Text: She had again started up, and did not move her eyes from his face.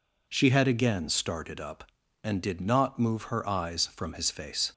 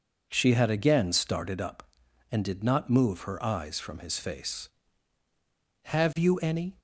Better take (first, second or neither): first